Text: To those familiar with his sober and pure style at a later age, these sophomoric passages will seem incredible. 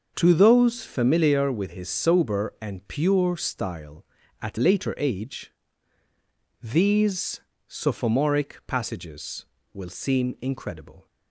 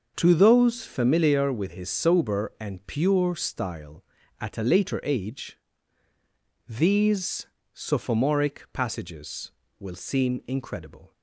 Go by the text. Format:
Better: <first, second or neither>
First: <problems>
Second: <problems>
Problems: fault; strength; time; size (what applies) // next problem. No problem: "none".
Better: second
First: starts louder than the rest; until 1.1 s; 6.5 dB // skips "a"; at 4.5 s // pauses between "these" and "sophomoric"; slight; at 7.4 s; 0.26 s long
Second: starts louder than the rest; until 1.1 s; 6.5 dB // pauses between "these" and "sophomoric"; slight; at 7.4 s; 0.26 s long